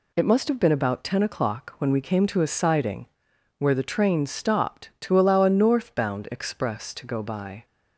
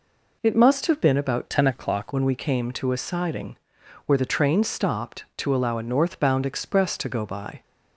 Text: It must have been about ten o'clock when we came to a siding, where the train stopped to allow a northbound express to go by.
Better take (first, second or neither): first